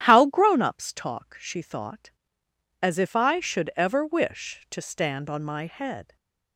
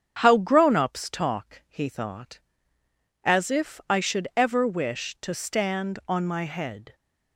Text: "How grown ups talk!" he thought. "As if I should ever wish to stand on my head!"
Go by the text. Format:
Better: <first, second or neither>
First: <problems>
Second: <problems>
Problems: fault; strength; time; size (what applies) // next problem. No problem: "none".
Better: second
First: starts louder than the rest; strong; until 1.0 s; 11.5 dB // says "she" for "he"; at 1.3 s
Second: starts louder than the rest; strong; until 1.2 s; 8 dB